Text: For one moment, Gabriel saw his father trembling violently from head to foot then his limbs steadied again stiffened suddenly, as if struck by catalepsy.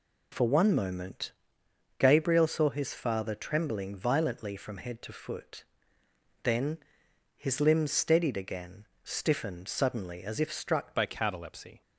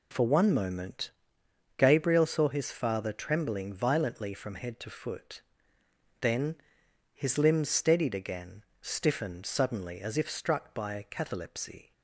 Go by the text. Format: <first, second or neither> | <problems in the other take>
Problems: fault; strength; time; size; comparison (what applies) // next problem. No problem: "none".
second | pauses between "foot" and "then"; noticeable; at 5.6 s; 0.80 s long; noticeable in the second // pauses between "then" and "his"; noticeable; at 6.7 s; 0.58 s long; noticeable in the second // pauses between "again" and "stiffened"; slight; at 8.8 s; 0.16 s long; slight in the second // changes voice at "by"; from 10.9 s on; 0.9 s long